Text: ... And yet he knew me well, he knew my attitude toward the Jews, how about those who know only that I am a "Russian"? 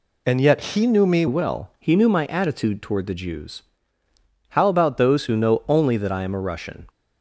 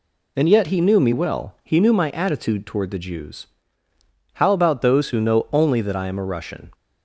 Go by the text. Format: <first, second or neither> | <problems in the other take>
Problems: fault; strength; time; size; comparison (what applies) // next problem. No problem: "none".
second | changes voice from "And" to "me"; from 0.2 to 1.2 s; 1.0 s long